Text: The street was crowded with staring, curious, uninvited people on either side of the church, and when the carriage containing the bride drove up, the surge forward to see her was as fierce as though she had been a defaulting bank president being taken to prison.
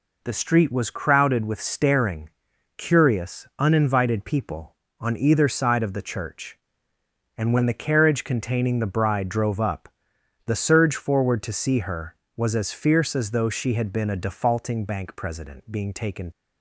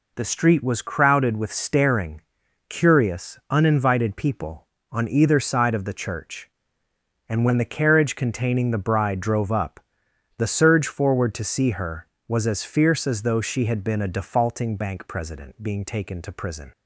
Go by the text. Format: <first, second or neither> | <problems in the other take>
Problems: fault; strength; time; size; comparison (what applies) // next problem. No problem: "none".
second | stops before "to prison"; at 16.3 s